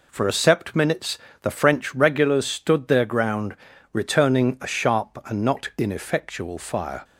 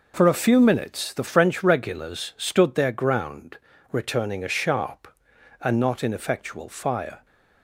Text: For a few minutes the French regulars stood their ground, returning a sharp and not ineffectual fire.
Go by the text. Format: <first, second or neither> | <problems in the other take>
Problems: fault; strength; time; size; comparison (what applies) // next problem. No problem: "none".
second | says "sept" for "few"; at 0.3 s // pauses between "minutes" and "the"; slight; at 1.1 s; 0.24 s long